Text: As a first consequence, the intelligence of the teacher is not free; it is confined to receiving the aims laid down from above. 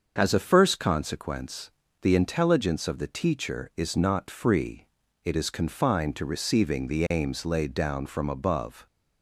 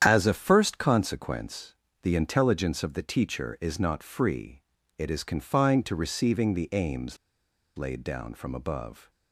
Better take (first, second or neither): first